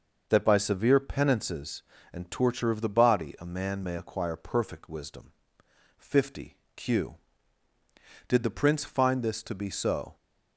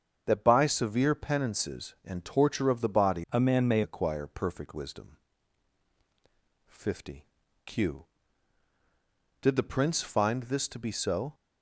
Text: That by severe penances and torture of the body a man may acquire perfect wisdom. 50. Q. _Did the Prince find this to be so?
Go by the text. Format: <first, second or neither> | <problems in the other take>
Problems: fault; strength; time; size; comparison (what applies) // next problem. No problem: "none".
first | starts louder than the rest; strong; until 1.2 s; 7 dB // changes voice from "a" to "may"; from 3.3 to 3.8 s; 0.5 s long